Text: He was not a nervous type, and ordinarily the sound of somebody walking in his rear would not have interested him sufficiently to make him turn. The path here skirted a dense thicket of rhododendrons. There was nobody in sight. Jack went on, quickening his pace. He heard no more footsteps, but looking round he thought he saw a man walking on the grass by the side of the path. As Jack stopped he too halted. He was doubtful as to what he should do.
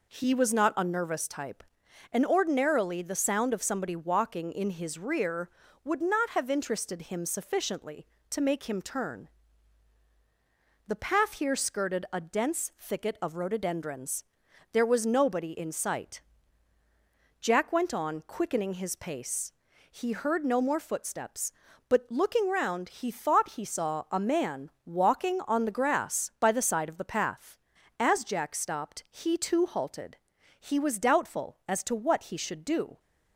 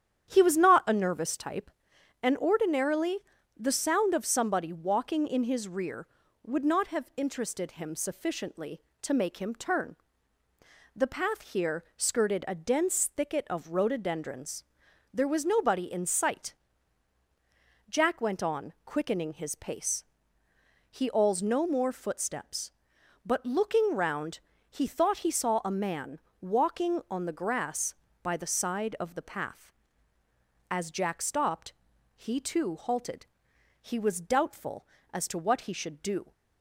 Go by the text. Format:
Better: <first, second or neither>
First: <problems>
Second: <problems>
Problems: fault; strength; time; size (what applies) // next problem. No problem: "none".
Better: first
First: pauses between "man" and "walking"; slight; at 24.7 s; 0.16 s long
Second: starts louder than the rest; strong; until 1.3 s; 9.5 dB // pauses between "ordinarily" and "the"; at 3.1 s; 0.40 s long // says "awls" for "heard"; at 21.0 s // pauses between "round" and "he"; slight; at 24.3 s; 0.30 s long // pauses between "man" and "walking"; slight; at 26.1 s; 0.20 s long // pauses between "stopped" and "he"; at 31.7 s; 0.42 s long